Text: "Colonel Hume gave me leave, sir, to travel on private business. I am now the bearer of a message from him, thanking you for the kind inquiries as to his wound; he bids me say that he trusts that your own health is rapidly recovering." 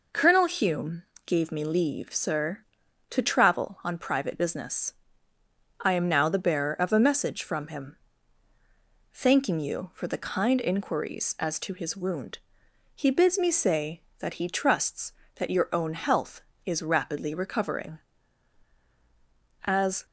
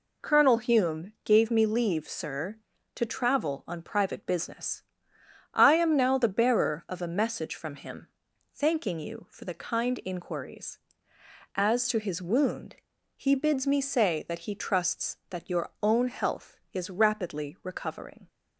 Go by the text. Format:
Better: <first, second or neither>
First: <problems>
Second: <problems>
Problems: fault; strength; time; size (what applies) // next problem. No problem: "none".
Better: second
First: pauses between "Hume" and "gave"; slight; at 1.0 s; 0.24 s long // goes on to say "As"; slight; from 19.6 s on; 0.40 s long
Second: none